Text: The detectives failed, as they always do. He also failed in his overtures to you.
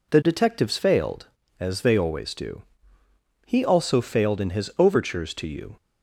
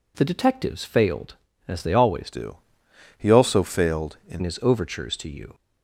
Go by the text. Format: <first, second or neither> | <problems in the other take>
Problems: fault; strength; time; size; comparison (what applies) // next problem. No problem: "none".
first | changes voice from "do" to "in"; from 2.3 to 4.4 s; 2.1 s long